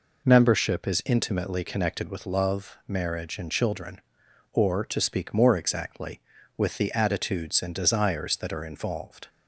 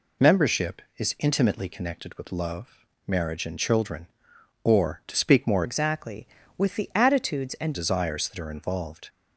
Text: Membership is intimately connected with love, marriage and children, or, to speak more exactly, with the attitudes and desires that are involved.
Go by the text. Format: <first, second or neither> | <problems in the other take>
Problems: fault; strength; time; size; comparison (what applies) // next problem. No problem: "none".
first | changes voice from "exactly" to "and"; from 5.6 to 7.7 s; 2.1 s long